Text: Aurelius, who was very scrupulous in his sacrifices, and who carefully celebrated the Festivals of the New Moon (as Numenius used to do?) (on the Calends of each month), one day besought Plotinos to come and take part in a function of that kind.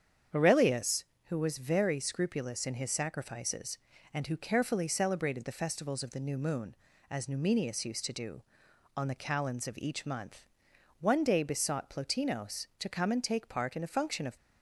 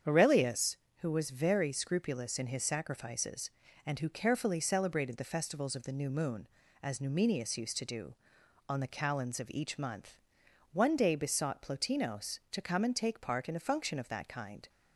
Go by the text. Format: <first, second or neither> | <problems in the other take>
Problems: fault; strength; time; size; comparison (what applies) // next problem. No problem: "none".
second | starts louder than the rest; strong; until 1.5 s; 8 dB; strong in the second // stops before "that kind"; at 14.3 s